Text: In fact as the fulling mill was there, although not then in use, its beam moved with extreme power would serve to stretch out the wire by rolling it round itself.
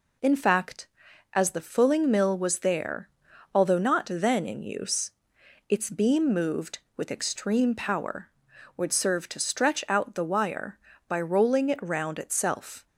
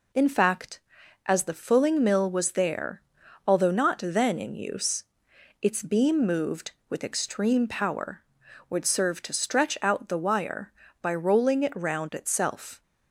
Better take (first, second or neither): neither